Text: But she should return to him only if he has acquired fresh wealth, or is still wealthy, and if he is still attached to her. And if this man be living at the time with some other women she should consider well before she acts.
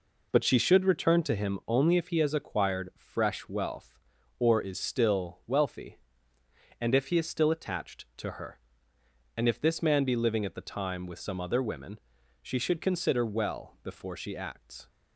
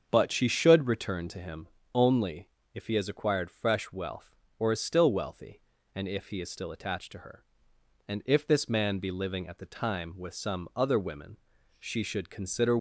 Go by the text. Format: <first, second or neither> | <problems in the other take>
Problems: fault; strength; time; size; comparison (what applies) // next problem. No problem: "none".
first | starts louder than the rest; until 1.1 s; 7 dB // pauses between "him" and "only"; slight; at 1.6 s; 0.26 s long // pauses between "only" and "if"; slight; at 2.4 s; 0.26 s long // pauses between "women" and "she"; at 11.3 s; 0.44 s long; also in the first // stops before "well before she acts"; at 12.7 s